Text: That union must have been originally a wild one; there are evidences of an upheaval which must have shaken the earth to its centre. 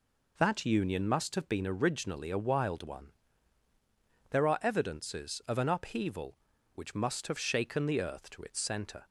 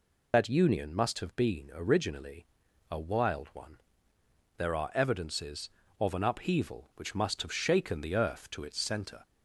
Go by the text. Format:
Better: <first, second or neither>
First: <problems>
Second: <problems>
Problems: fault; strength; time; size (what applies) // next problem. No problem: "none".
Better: first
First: none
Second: loses the start of "That"; at 0.3 s; 65 ms // pauses between "originally" and "a"; at 2.4 s; 0.44 s long